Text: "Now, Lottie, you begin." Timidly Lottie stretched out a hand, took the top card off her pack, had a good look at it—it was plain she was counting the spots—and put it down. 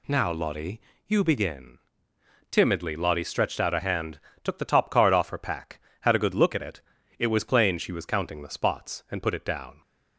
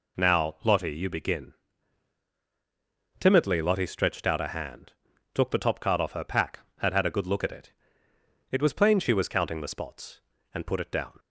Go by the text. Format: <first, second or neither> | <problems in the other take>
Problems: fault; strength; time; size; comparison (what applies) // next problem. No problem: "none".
first | says "had" twice; at 6.9 s